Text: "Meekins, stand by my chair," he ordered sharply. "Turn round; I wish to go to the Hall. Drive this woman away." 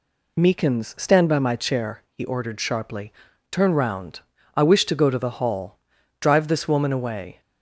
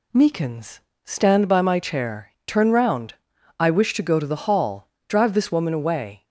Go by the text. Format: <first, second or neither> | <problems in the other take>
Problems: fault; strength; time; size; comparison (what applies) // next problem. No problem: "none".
first | skips "he ordered sharply"; at 2.3 s